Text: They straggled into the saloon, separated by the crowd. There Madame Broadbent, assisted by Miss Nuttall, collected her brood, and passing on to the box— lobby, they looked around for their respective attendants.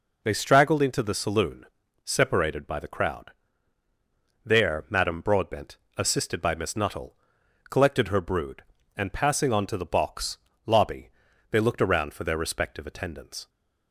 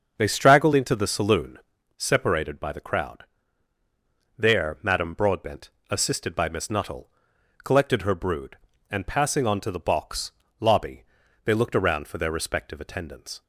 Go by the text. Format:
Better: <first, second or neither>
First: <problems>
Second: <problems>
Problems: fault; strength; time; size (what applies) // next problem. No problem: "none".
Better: first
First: none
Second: starts louder than the rest; until 1.8 s; 6.5 dB